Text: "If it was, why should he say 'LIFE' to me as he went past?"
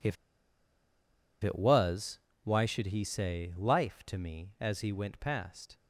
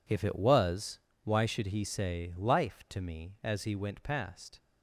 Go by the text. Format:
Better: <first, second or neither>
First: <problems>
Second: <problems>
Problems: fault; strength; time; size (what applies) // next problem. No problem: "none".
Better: second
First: pauses between "If" and "it"; strong; at 0.1 s; 1.2 s long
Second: none